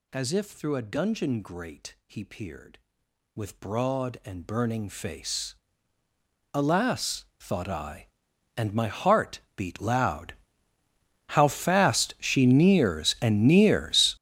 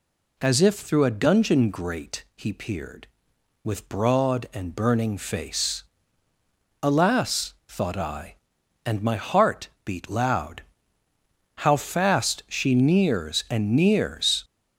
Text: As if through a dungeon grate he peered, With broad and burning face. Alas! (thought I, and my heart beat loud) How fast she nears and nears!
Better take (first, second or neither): second